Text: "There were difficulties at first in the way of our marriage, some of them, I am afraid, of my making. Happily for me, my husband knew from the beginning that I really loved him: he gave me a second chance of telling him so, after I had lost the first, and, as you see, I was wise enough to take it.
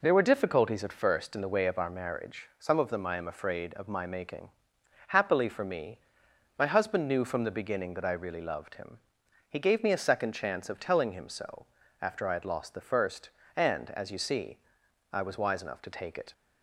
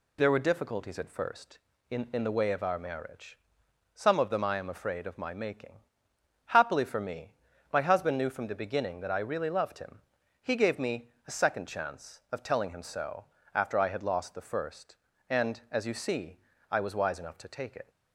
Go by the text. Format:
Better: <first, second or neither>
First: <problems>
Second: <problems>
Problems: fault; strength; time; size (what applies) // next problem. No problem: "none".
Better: first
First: none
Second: says "in" twice; at 2.1 s // pauses between "me" and "a"; slight; at 11.0 s; 0.16 s long